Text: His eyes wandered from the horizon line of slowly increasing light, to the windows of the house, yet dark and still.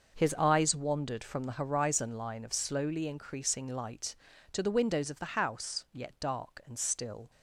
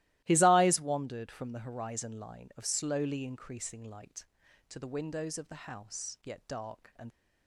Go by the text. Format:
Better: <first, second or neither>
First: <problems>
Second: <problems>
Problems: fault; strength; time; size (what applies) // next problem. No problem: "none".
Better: first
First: starts louder than the rest; noticeable; until 1.2 s; 6 dB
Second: starts louder than the rest; strong; until 1.2 s; 16.5 dB // stops before "still"; at 7.1 s